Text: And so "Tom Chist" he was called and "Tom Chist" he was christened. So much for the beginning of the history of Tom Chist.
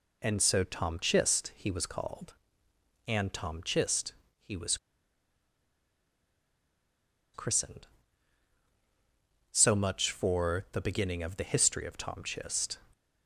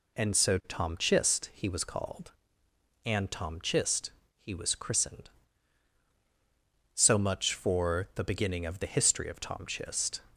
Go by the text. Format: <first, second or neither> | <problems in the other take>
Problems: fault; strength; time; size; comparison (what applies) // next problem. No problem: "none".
second | pauses between "Chist" and "he"; slight; at 4.1 s; 0.28 s long; slight in the second // pauses between "was" and "christened"; strong; at 4.7 s; 2.5 s long